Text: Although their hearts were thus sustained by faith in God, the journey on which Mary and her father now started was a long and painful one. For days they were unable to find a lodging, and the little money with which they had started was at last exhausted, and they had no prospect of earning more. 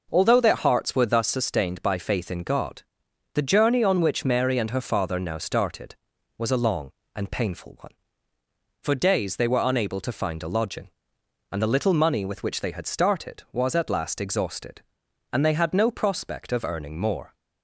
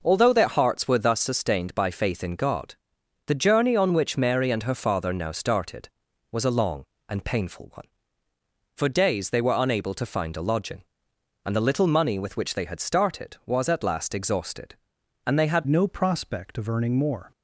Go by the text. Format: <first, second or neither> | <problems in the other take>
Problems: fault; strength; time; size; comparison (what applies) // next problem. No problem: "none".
first | changes voice at "no"; from 15.6 s on; 1.7 s long